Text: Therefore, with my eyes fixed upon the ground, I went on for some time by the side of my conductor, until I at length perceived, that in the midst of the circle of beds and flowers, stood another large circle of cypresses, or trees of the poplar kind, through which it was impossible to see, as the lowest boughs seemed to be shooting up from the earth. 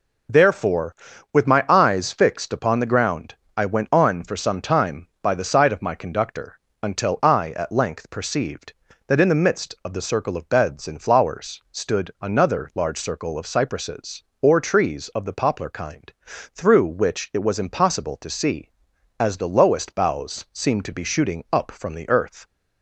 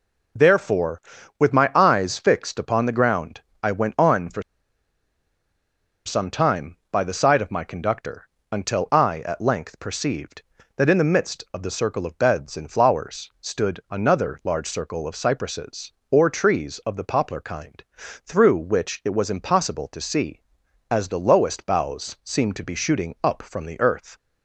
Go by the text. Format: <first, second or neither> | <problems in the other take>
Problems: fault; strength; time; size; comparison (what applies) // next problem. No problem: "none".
first | pauses between "for" and "some"; strong; at 4.4 s; 1.6 s long